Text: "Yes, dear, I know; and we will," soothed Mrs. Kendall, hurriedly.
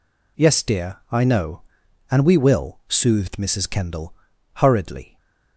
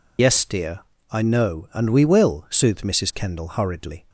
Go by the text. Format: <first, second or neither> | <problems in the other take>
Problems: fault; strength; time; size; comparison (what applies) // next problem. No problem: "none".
first | loses the start of "Yes"; at 0.1 s; 90 ms